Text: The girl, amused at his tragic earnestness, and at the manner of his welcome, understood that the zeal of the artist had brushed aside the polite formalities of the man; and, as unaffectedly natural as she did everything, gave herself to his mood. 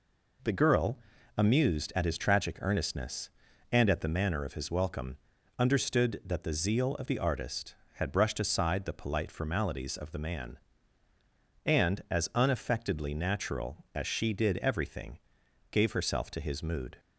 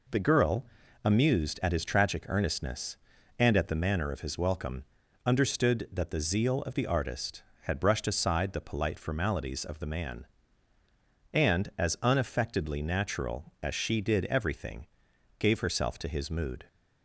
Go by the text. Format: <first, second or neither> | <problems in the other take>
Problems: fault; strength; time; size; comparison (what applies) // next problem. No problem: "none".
neither | none